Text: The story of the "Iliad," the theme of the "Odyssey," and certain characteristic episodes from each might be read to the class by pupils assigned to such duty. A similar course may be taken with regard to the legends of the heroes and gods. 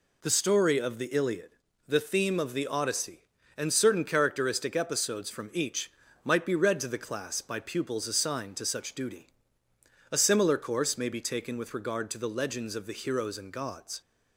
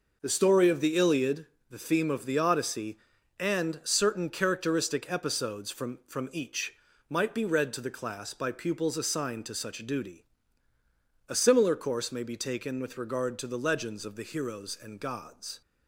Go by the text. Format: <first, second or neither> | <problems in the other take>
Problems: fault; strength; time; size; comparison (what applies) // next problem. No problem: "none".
first | says "from" twice; at 6.0 s // pauses between "each" and "might"; slight; at 6.7 s; 0.36 s long; slight in the first